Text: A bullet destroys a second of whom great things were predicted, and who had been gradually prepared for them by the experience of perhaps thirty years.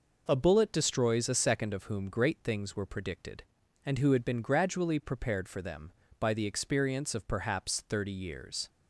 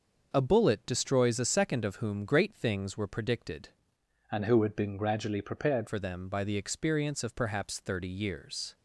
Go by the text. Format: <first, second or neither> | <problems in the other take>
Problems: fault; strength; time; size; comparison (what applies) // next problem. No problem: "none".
first | starts louder than the rest; until 1.3 s; 6 dB // changes voice from "and" to "prepared"; from 4.3 to 5.8 s; 1.5 s long